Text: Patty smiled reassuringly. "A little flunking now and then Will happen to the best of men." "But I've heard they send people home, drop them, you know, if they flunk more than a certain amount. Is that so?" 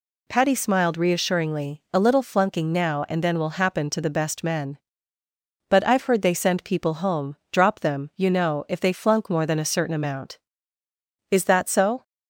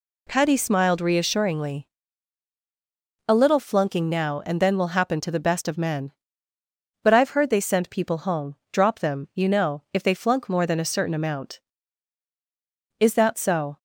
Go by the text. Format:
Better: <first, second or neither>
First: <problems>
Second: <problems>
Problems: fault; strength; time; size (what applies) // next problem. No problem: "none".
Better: second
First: skips "of"; at 4.4 s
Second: none